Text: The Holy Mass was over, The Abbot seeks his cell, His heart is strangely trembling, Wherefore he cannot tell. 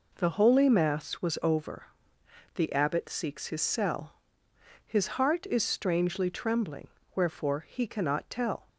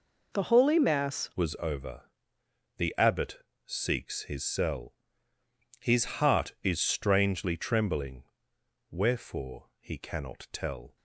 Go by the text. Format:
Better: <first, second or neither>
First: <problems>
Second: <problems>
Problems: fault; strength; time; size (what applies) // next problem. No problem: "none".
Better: first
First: none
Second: changes voice at "was"; from 1.3 s on; 9.6 s long // pauses between "Abbot" and "seeks"; slight; at 3.4 s; 0.22 s long